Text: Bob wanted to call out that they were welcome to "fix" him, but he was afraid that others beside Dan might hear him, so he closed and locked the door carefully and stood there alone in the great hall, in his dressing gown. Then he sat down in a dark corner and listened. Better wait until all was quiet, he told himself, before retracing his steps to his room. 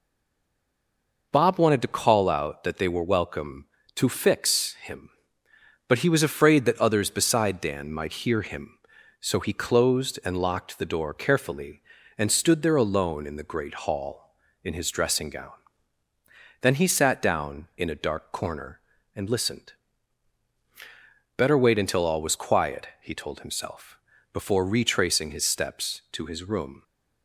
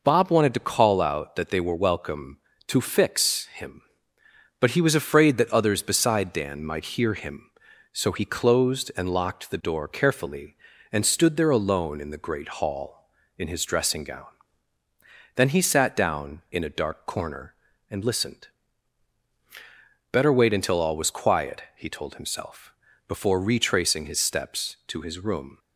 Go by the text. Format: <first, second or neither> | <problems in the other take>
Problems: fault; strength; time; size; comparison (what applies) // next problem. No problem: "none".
second | stays silent before the first word; noticeable; until 1.3 s; 1.3 s long